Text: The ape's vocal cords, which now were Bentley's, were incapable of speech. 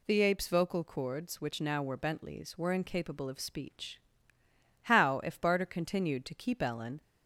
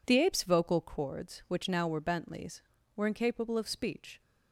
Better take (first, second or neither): second